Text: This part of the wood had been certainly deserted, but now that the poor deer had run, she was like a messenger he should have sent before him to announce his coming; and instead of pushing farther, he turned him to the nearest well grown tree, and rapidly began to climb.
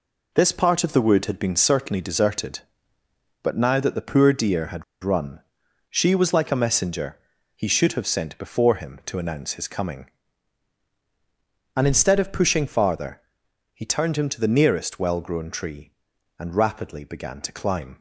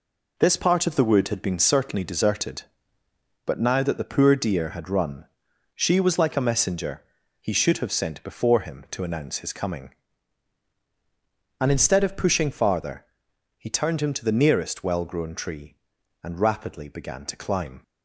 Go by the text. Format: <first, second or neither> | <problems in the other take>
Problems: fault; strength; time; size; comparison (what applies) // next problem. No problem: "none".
second | pauses between "had" and "run"; slight; at 4.8 s; 0.20 s long // pauses between "messenger" and "he"; slight; at 7.1 s; 0.36 s long; slight in the second